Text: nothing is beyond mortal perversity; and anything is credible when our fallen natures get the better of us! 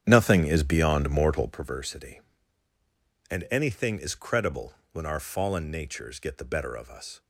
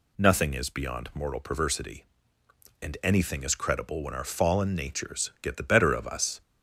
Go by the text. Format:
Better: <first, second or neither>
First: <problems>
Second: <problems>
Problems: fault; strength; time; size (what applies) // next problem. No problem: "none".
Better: second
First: starts louder than the rest; strong; until 1.7 s; 9 dB // pauses between "credible" and "when"; slight; at 4.7 s; 0.18 s long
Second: none